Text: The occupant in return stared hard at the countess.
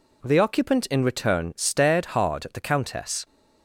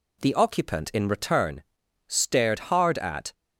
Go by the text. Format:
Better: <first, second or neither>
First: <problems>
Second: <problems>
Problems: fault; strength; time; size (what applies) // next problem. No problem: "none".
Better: first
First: none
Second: pauses between "return" and "stared"; at 1.6 s; 0.44 s long // stops before "the countess"; at 3.3 s